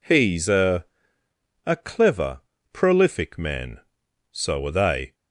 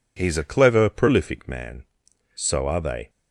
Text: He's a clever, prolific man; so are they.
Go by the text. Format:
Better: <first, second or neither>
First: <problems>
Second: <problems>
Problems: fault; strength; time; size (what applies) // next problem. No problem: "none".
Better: second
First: says "a" twice; at 1.6 s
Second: none